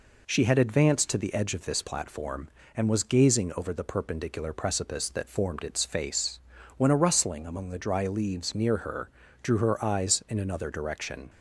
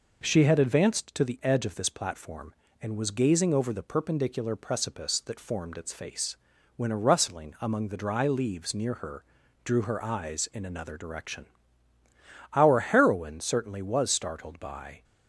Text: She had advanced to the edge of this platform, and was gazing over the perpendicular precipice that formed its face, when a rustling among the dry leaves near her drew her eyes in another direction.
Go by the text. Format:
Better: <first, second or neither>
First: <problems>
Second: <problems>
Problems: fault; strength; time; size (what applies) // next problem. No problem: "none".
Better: first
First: pauses between "her" and "drew"; slight; at 9.0 s; 0.32 s long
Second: pauses between "her" and "drew"; at 9.2 s; 0.42 s long // goes on to say "Our heroine certainly was startled by"; strong; from 12.5 s on; 2.5 s long